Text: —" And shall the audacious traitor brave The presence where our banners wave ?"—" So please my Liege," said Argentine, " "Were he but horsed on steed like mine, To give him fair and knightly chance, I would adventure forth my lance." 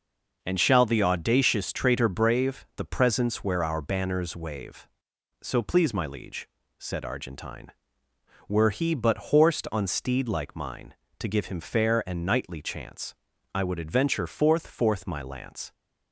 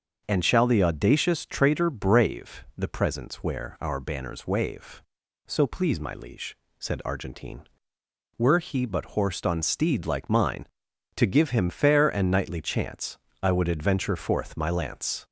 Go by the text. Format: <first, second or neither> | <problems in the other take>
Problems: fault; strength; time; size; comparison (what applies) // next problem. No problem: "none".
second | starts louder than the rest; until 1.4 s; 7 dB; strong in the second // says "forth" twice; at 14.6 s